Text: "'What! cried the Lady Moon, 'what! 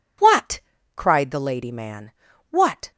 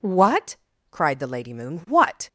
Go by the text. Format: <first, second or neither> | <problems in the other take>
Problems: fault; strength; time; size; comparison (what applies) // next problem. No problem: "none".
second | says "Man" for "Moon"; at 1.7 s